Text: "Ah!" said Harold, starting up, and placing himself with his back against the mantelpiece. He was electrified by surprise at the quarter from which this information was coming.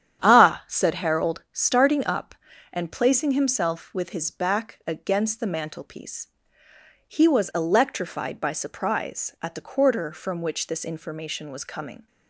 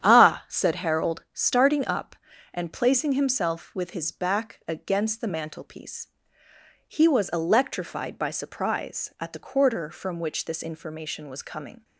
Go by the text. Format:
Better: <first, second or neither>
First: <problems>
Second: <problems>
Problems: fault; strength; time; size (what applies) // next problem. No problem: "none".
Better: neither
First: starts louder than the rest; strong; until 1.2 s; 9 dB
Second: starts louder than the rest; strong; until 1.0 s; 9 dB